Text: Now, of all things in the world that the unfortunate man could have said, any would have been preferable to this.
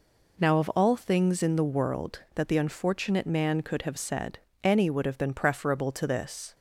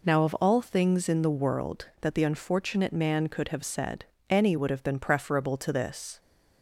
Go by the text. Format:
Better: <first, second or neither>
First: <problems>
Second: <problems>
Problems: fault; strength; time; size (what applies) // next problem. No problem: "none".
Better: neither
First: none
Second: none